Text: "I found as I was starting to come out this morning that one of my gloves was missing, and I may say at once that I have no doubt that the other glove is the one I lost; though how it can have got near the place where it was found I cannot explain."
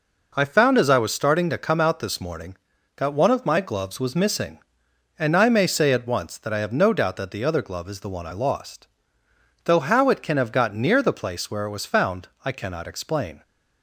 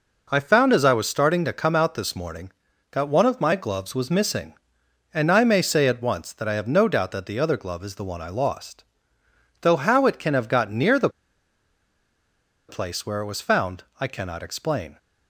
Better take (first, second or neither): first